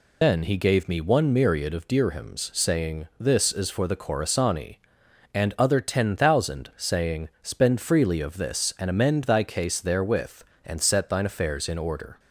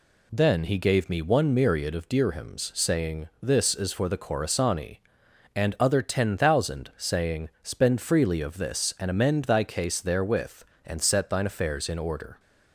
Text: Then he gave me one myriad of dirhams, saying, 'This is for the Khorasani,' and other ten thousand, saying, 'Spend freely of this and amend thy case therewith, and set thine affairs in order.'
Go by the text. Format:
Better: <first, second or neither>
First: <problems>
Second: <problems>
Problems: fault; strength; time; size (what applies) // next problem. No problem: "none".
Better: second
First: loses the start of "Then"; at 0.2 s; 110 ms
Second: none